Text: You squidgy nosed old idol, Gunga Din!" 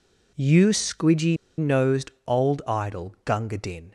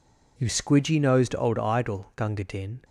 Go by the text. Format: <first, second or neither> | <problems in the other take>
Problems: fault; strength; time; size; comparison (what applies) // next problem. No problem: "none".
second | pauses between "squidgy" and "nosed"; slight; at 1.3 s; 0.22 s long // pauses between "nosed" and "old"; slight; at 2.1 s; 0.16 s long